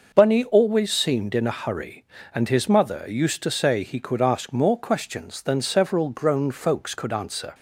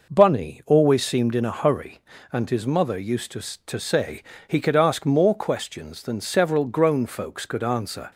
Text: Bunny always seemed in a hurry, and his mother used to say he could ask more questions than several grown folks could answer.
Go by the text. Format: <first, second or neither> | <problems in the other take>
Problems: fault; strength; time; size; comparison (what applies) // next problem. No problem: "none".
first | says "to" twice; at 3.6 s // pauses between "say" and "he"; slight; at 4.2 s; 0.25 s long